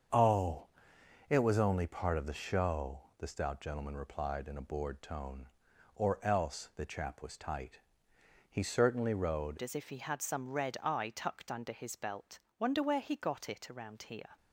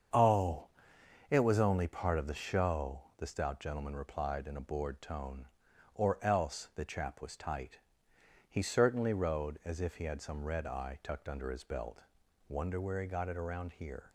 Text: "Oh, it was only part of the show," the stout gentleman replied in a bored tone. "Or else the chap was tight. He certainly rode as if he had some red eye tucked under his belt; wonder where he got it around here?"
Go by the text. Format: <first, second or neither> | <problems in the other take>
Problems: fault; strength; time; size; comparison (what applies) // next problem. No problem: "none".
second | starts louder than the rest; strong; until 1.7 s; 7 dB; strong in the second // changes voice at "as"; from 9.6 s on; 4.7 s long